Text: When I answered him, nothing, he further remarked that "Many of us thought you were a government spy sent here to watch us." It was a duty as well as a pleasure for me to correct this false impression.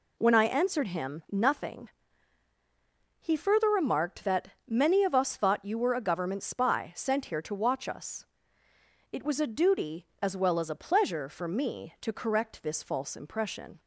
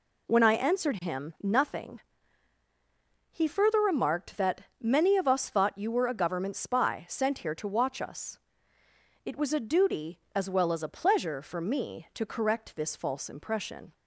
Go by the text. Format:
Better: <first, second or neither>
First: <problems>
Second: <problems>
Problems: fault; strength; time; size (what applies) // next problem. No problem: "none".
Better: neither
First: pauses between "that" and "Many"; slight; at 4.5 s; 0.16 s long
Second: pauses between "that" and "Many"; slight; at 4.6 s; 0.16 s long